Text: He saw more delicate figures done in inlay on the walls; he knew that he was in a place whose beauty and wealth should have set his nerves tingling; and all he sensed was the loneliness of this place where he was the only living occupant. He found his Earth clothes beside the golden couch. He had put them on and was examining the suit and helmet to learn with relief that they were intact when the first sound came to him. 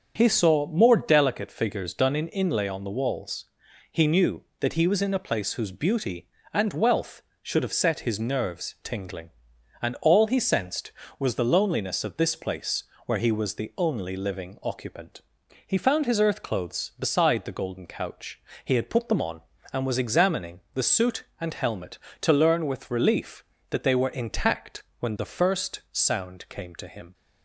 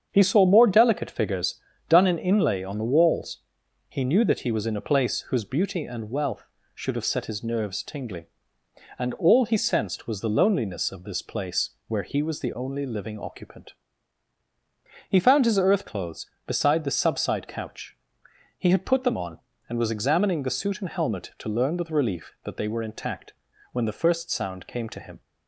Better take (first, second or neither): first